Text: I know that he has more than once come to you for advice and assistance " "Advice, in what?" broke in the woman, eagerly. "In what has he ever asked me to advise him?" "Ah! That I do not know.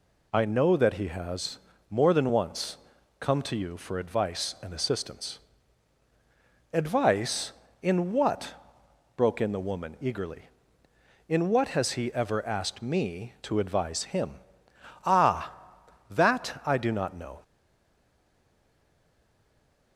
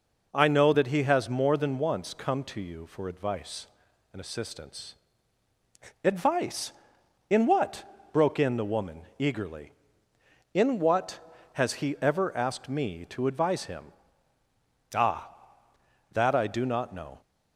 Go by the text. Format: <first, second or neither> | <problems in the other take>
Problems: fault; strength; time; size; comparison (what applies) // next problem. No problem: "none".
second | pauses between "has" and "more"; slight; at 1.5 s; 0.32 s long // pauses between "once" and "come"; at 2.7 s; 0.42 s long // stays silent after the last word; from 17.4 s on; 2.5 s long